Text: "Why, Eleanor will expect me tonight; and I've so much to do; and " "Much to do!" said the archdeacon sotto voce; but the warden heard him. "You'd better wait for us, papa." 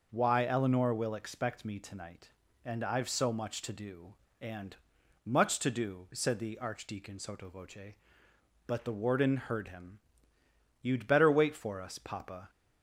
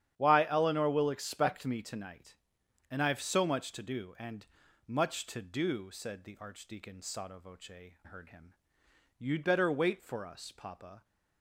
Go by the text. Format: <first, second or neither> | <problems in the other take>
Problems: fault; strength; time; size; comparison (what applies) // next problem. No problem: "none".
first | starts louder than the rest; strong; until 1.1 s; 11 dB // skips "but the warden"; at 7.9 s